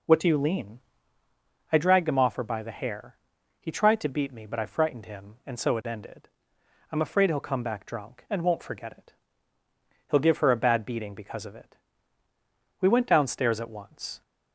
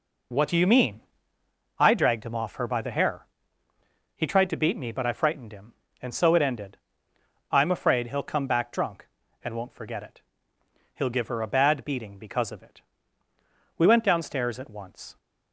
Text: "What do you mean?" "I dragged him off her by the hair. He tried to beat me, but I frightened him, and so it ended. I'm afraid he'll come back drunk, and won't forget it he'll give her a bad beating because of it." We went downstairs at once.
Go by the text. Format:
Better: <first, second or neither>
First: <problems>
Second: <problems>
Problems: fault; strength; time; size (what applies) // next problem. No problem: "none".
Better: second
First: says "lean" for "mean"; at 0.3 s // pauses between "it" and "he'll"; noticeable; at 9.1 s; 0.96 s long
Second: pauses between "it" and "he'll"; noticeable; at 10.2 s; 0.74 s long